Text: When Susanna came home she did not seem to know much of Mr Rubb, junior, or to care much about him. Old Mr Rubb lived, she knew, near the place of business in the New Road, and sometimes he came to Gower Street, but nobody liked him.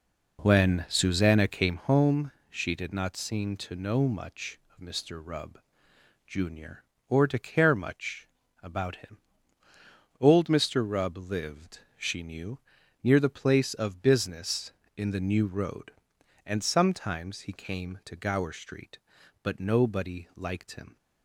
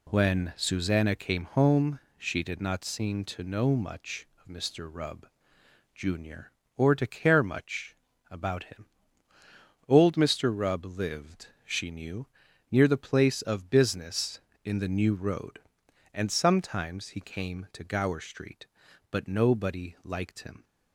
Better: second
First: starts louder than the rest; noticeable; until 1.9 s; 4.5 dB // pauses between "home" and "she"; slight; at 2.3 s; 0.16 s long // pauses between "much" and "about"; at 8.2 s; 0.38 s long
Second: pauses between "home" and "she"; slight; at 1.9 s; 0.16 s long // pauses between "much" and "about"; at 7.9 s; 0.38 s long

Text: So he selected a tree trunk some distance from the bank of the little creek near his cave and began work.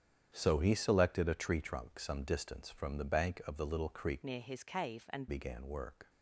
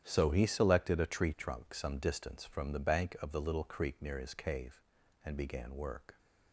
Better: second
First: starts louder than the rest; strong; until 1.3 s; 9.5 dB // changes voice from "near" to "and"; from 4.2 to 5.2 s; 1.0 s long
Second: starts louder than the rest; strong; until 1.0 s; 10.5 dB

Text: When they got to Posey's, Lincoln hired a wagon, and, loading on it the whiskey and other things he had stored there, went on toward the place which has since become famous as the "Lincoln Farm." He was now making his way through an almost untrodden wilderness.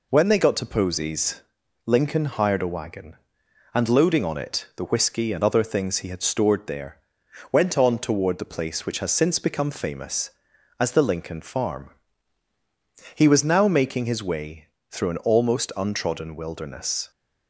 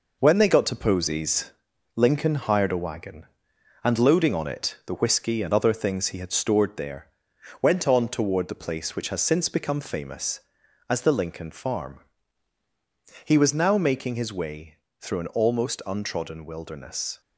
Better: first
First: pauses between "way" and "through"; slight; at 14.6 s; 0.24 s long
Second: gets quieter; noticeable; throughout; 6 dB // pauses between "way" and "through"; slight; at 14.7 s; 0.24 s long

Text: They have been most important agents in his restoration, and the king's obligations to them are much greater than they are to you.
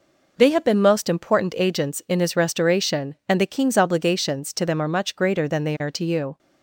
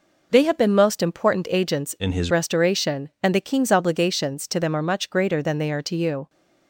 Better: first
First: none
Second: changes voice from "in" to "his"; from 1.9 to 2.3 s; 0.4 s long

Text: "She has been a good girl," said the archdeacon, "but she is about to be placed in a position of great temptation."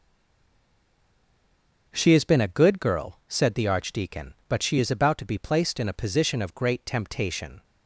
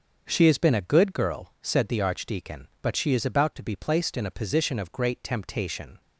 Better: second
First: stays silent before the first word; noticeable; until 1.9 s; 1.9 s long // starts louder than the rest; until 2.9 s; 7 dB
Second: starts louder than the rest; until 1.2 s; 7 dB

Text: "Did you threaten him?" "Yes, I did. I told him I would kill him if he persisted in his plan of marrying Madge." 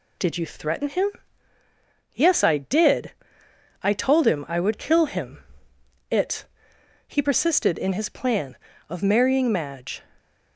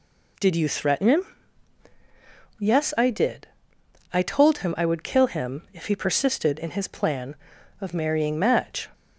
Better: second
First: says "it" for "if"; at 6.1 s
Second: none

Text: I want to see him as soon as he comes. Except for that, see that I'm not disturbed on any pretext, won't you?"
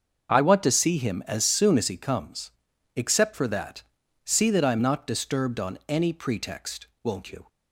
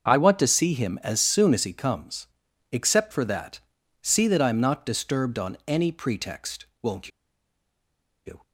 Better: first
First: starts louder than the rest; until 1.3 s; 6.5 dB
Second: starts louder than the rest; until 1.1 s; 6.5 dB // pauses between "won't" and "you"; at 7.1 s; 1.1 s long

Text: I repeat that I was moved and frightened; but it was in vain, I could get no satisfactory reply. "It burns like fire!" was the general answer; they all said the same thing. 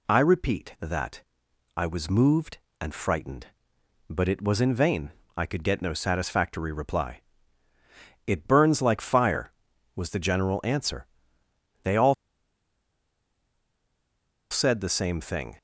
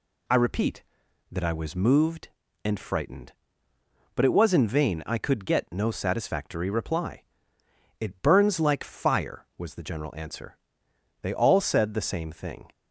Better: second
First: pauses between "that" and "I"; noticeable; at 1.2 s; 0.54 s long // pauses between "all" and "said"; strong; at 12.1 s; 2.3 s long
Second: none

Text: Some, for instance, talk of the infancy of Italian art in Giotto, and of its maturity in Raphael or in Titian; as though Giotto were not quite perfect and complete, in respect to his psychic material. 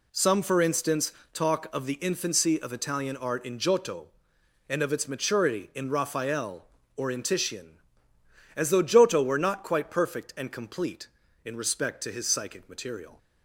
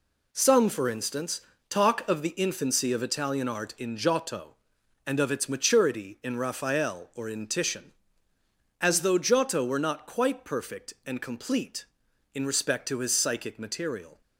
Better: neither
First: none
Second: none

